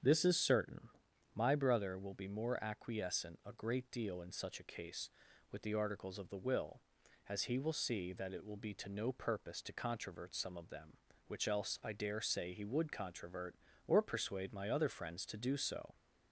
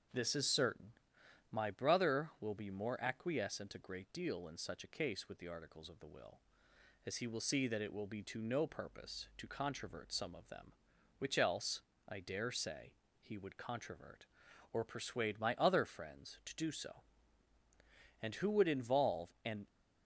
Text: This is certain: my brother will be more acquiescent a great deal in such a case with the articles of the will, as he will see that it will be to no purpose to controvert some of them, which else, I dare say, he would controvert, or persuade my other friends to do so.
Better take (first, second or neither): first